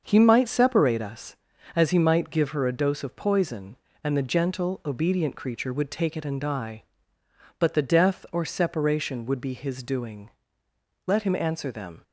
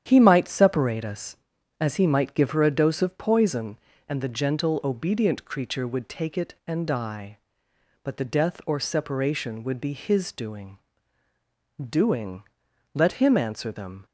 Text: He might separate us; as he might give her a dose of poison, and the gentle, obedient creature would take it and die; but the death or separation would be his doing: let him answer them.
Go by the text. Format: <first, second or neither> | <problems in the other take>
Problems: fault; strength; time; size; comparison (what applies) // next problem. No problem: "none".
first | starts louder than the rest; strong; until 1.0 s; 9.5 dB; also in the first // says "doing" twice; at 11.8 s